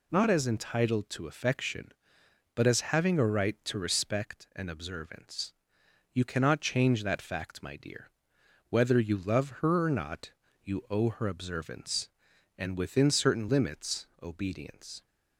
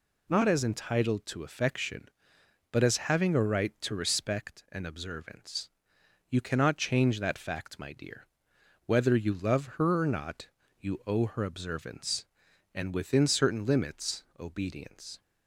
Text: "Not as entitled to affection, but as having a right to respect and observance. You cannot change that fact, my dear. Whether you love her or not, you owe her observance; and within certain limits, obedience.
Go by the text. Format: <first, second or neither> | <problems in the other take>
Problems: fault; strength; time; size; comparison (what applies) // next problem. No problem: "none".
neither | none